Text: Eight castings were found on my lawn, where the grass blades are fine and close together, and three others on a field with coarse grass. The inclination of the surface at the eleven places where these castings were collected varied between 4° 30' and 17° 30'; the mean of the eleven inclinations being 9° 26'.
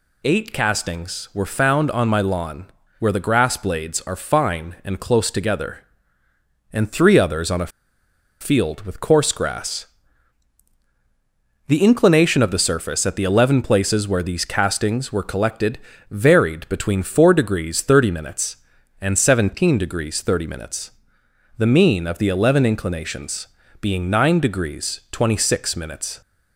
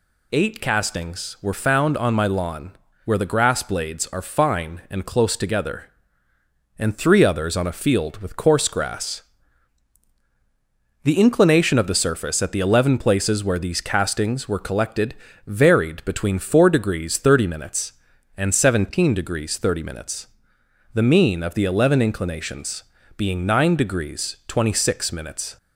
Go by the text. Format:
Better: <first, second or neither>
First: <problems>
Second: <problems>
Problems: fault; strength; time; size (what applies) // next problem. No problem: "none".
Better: second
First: pauses between "a" and "field"; noticeable; at 7.7 s; 0.71 s long // pauses between "collected" and "varied"; slight; at 15.7 s; 0.32 s long // pauses between "inclinations" and "being"; slight; at 23.4 s; 0.36 s long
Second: pauses between "collected" and "varied"; slight; at 15.1 s; 0.32 s long // pauses between "inclinations" and "being"; slight; at 22.8 s; 0.36 s long